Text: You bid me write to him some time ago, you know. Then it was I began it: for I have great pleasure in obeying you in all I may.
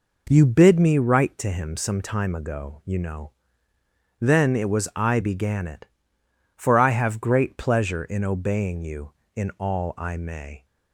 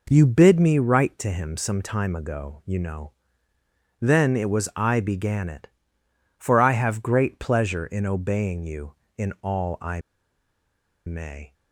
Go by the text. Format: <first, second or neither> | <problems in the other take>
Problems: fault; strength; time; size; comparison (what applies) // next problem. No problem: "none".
first | pauses between "I" and "may"; at 10.0 s; 1.0 s long